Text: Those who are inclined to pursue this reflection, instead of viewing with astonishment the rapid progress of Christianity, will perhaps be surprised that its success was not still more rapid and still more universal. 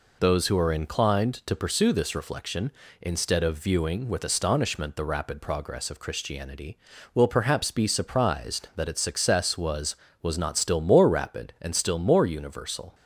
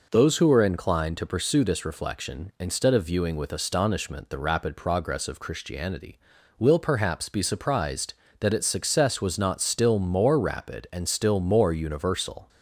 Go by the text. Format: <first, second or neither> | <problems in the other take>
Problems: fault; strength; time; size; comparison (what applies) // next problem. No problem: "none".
second | says "was" twice; at 10.2 s